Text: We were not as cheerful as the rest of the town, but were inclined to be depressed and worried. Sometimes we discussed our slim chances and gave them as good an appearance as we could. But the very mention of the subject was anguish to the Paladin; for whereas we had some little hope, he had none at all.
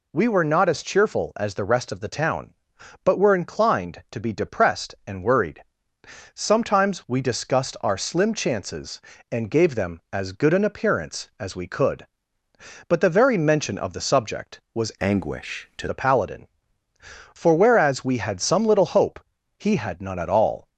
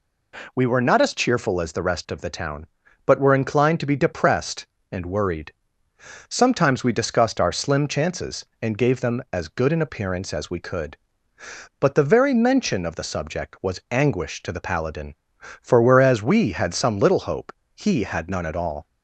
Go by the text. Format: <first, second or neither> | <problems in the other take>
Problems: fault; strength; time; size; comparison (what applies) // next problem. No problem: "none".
second | changes voice from "anguish" to "to"; from 15.0 to 15.8 s; 0.8 s long